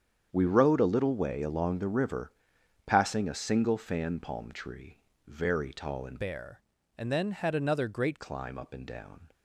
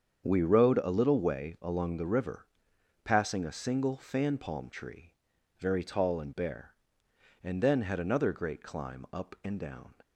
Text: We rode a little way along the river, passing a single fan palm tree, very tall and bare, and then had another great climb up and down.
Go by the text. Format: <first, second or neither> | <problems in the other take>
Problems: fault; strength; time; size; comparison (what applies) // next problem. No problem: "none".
second | starts louder than the rest; strong; until 1.3 s; 8 dB; strong in the second // changes voice from "bare" to "great"; from 6.2 to 8.1 s; 1.9 s long